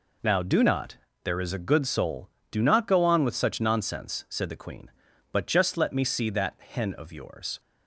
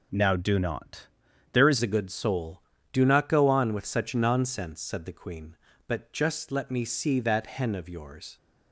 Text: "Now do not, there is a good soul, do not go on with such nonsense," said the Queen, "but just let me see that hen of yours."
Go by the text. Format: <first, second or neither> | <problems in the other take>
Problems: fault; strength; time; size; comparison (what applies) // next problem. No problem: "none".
first | changes voice at "a"; from 1.8 s on; 6.5 s long